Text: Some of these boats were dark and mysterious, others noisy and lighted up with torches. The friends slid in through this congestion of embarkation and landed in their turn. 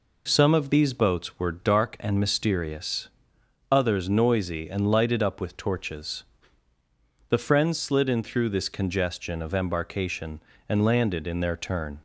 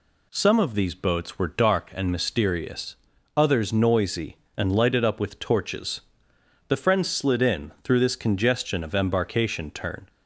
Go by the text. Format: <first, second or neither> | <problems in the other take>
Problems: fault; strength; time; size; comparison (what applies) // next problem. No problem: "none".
first | skips "and landed in their"; at 9.7 s